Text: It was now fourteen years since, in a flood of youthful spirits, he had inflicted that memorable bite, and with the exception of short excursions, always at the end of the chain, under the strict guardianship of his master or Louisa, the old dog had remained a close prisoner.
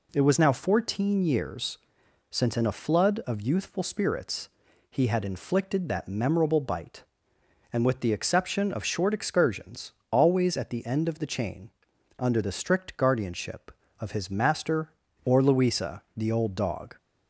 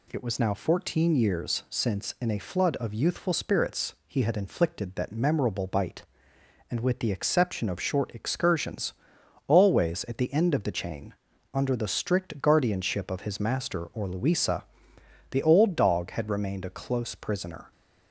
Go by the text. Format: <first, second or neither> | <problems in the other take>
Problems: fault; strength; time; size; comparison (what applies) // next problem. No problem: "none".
second | pauses between "years" and "since"; noticeable; at 1.7 s; 0.52 s long // stops before "had remained a close prisoner"; at 16.9 s